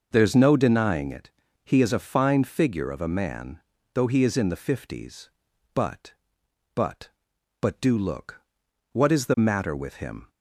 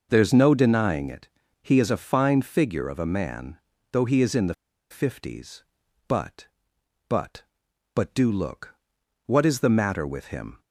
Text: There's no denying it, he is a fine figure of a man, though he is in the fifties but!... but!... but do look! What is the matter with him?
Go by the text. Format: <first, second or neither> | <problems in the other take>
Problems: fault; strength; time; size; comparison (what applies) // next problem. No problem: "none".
first | pauses between "the" and "fifties"; at 4.5 s; 0.37 s long